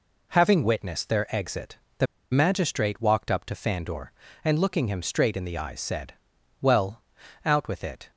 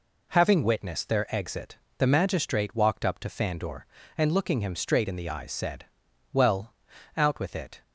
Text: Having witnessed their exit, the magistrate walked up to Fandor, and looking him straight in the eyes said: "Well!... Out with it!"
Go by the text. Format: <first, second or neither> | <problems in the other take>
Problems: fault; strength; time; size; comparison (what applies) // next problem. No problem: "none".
second | pauses between "the" and "magistrate"; slight; at 2.0 s; 0.26 s long